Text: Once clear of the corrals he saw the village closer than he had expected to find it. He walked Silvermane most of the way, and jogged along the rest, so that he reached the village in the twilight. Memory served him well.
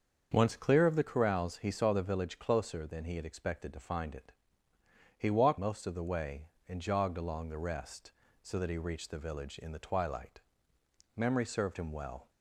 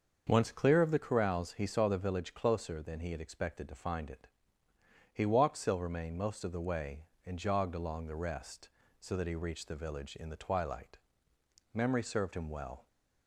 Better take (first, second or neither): second